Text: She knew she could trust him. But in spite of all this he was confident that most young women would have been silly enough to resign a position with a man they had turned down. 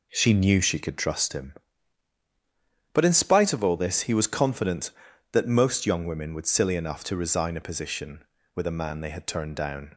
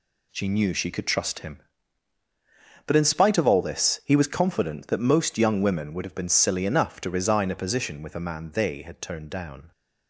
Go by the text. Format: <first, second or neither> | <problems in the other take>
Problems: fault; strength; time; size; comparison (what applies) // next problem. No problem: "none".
second | skips "have been"; at 6.4 s